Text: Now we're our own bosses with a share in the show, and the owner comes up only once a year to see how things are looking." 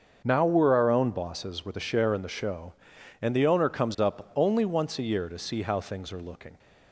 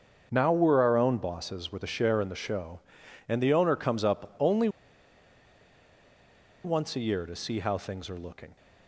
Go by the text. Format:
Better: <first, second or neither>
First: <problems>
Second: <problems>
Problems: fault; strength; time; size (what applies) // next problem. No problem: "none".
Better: first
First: starts louder than the rest; until 1.2 s; 7 dB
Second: starts louder than the rest; until 1.3 s; 6.5 dB // pauses between "only" and "once"; strong; at 4.6 s; 1.9 s long